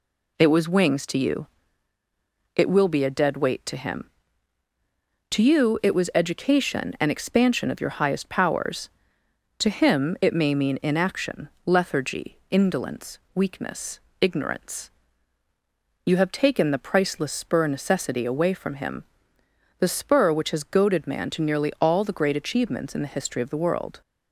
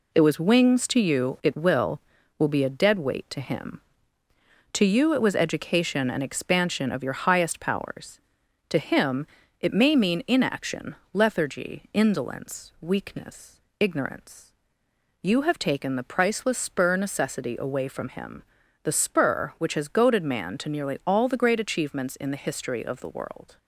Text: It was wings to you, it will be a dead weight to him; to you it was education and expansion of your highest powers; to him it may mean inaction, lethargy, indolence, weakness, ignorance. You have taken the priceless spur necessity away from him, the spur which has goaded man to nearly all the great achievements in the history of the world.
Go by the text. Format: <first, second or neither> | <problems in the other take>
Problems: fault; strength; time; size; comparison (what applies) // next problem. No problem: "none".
first | says "will" twice; at 2.3 s // pauses between "him" and "it"; slight; at 9.2 s; 0.32 s long